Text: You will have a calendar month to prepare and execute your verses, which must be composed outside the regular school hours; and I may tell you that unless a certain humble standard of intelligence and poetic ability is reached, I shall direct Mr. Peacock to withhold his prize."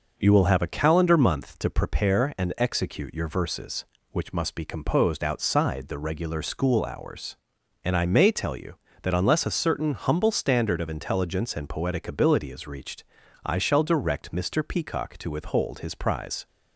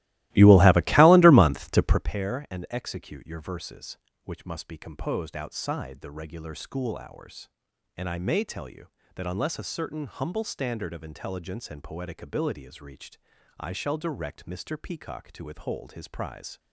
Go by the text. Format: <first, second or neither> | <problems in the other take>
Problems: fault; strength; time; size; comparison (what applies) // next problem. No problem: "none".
first | starts louder than the rest; strong; until 2.2 s; 17.5 dB